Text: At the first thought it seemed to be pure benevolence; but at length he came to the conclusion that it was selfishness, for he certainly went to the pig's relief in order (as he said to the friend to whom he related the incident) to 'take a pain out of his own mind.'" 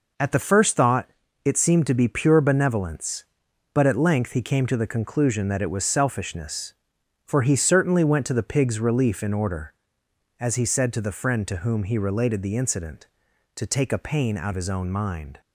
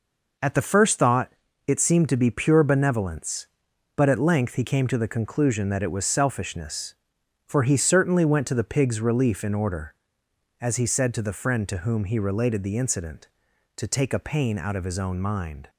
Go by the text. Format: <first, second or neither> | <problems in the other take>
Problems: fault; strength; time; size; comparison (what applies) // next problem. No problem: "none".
second | pauses between "thought" and "it"; slight; at 1.0 s; 0.34 s long; slight in the second // skips "of"; at 14.5 s